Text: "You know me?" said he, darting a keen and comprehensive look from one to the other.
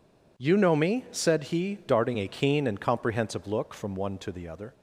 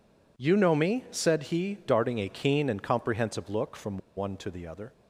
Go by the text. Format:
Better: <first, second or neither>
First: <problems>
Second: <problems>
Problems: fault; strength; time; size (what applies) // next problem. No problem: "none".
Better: first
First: none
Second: pauses between "from" and "one"; slight; at 3.9 s; 0.18 s long